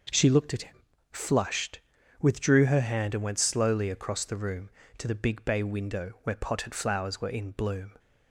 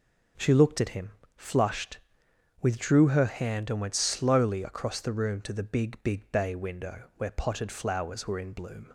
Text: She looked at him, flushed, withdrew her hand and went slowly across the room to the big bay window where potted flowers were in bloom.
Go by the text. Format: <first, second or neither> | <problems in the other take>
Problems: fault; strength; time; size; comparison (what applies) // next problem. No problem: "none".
first | says "big" twice; at 6.0 s